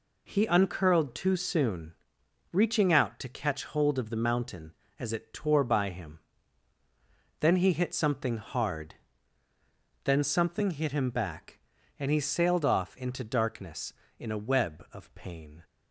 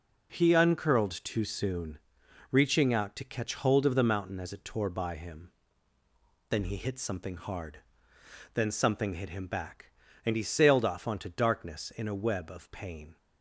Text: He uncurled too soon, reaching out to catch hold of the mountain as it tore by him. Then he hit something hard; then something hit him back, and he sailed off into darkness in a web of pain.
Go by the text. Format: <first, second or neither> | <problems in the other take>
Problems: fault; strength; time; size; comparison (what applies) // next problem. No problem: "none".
first | says "onto" for "into"; at 11.0 s